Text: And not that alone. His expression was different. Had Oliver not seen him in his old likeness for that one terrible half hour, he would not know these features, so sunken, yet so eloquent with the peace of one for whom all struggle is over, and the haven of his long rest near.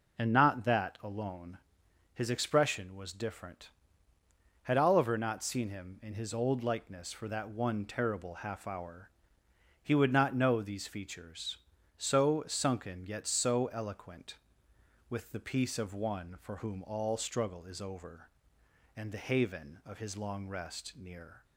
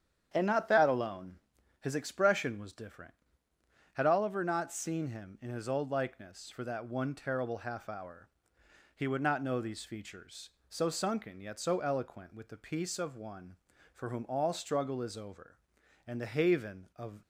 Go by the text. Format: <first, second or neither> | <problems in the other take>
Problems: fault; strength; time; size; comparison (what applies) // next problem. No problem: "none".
first | starts louder than the rest; strong; until 1.3 s; 9 dB // stops before "his long rest near"; at 17.2 s